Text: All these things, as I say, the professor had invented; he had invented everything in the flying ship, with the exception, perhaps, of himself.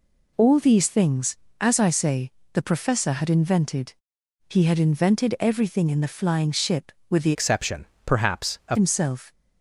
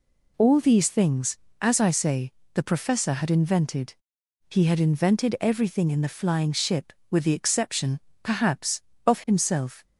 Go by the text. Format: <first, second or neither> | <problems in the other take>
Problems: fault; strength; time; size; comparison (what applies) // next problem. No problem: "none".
second | changes voice from "exception" to "of"; from 7.3 to 8.7 s; 1.4 s long